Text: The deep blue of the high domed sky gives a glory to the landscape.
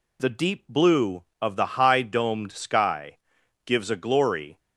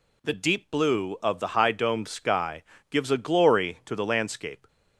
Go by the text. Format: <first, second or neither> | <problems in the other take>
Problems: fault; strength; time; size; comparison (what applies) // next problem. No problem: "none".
second | pauses between "sky" and "gives"; noticeable; at 3.1 s; 0.48 s long; slight in the second // stops before "to the landscape"; at 4.5 s